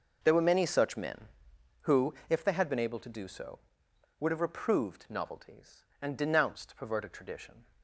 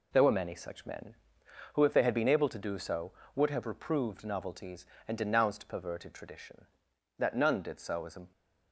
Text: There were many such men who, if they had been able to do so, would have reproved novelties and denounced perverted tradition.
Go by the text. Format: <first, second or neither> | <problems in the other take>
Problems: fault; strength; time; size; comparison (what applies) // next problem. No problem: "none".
first | goes on to say "That none did so is a"; noticeable; from 7.1 s on; 1.1 s long